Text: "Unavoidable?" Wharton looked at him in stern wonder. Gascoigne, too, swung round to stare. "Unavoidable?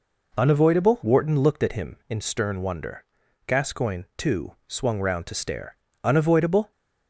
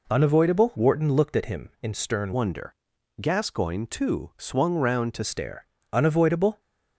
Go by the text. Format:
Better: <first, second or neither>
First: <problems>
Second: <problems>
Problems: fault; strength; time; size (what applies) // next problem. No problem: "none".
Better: first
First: none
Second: changes voice from "wonder" to "to"; from 2.3 to 5.2 s; 2.9 s long